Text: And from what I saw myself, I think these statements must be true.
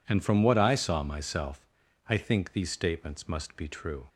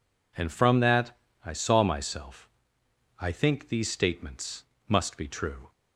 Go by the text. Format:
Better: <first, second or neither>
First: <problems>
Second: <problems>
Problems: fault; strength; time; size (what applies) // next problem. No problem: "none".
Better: first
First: none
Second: says "that" for "what"; at 0.7 s // pauses between "statements" and "must"; slight; at 4.6 s; 0.24 s long